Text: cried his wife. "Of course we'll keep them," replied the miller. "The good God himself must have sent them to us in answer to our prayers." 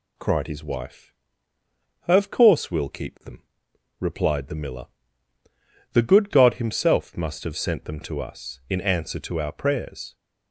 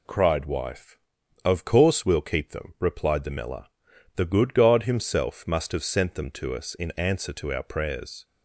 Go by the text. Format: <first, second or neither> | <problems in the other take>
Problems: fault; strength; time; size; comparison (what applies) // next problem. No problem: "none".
first | skips "his"; at 0.4 s